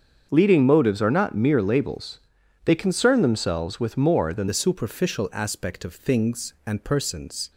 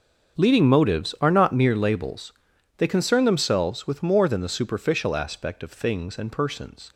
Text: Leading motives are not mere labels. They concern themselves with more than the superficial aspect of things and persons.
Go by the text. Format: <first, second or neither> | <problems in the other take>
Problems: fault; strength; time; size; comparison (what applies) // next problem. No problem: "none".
second | starts louder than the rest; until 1.3 s; 7 dB; also in the second // changes voice at "the"; from 4.4 s on; 3.1 s long